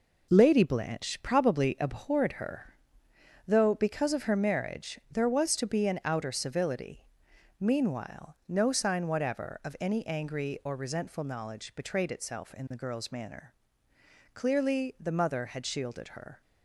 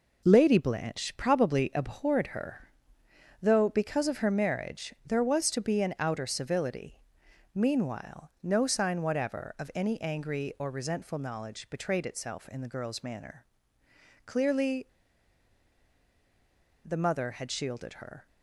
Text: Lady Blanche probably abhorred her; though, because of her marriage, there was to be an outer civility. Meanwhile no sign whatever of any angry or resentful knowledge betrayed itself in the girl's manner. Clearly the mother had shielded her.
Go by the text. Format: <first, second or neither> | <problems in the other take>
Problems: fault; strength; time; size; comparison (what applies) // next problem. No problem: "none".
first | pauses between "Clearly" and "the"; strong; at 14.8 s; 1.9 s long